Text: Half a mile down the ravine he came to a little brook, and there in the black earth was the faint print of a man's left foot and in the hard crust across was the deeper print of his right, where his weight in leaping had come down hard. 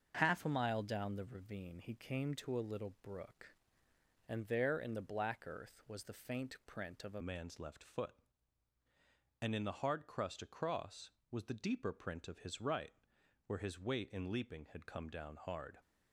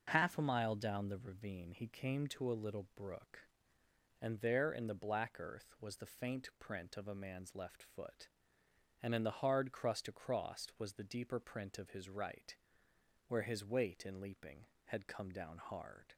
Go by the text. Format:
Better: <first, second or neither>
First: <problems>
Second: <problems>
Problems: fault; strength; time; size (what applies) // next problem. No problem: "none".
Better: second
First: starts louder than the rest; until 1.2 s; 6.5 dB // changes voice at "man's"; from 7.2 s on; 8.5 s long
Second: none